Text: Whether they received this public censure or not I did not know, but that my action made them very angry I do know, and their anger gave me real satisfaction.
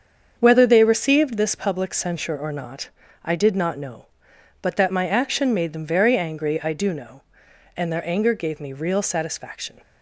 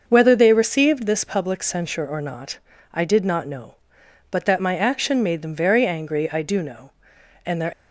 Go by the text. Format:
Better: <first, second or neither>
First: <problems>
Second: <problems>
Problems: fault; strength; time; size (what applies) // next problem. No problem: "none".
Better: first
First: starts louder than the rest; strong; until 1.3 s; 7 dB // pauses between "not" and "I"; slight; at 2.9 s; 0.34 s long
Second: starts louder than the rest; until 1.0 s; 6.5 dB // pauses between "not" and "I"; slight; at 2.5 s; 0.34 s long // stops before "anger gave me real satisfaction"; at 7.7 s